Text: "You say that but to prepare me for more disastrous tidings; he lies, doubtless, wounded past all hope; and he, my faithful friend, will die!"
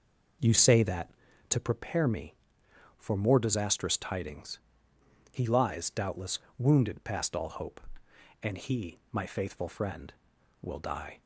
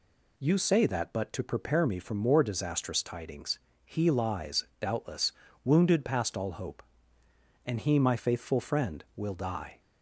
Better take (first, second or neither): second